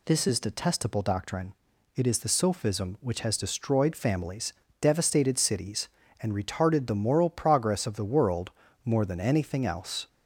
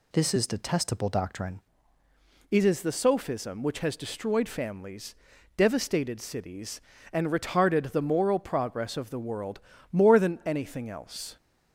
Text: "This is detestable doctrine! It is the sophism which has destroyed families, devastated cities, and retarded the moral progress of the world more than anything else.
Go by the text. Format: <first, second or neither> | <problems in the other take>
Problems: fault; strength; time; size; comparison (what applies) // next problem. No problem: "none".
first | changes voice at "It"; from 2.5 s on; 8.8 s long // pauses between "world" and "more"; slight; at 9.5 s; 0.32 s long; slight in the first